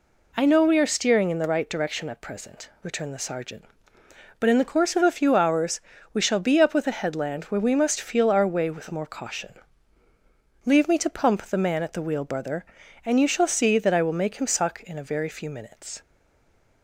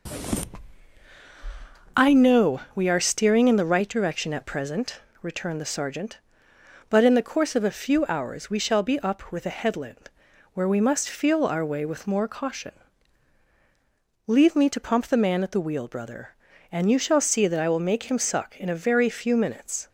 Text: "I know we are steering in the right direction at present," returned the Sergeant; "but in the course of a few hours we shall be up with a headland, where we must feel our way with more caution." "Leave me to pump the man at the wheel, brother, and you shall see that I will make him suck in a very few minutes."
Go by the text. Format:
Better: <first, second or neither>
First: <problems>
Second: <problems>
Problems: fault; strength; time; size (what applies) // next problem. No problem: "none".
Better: second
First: pauses between "hours" and "we"; slight; at 5.7 s; 0.36 s long // stays silent after the last word; slight; from 16.0 s on; 0.8 s long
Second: none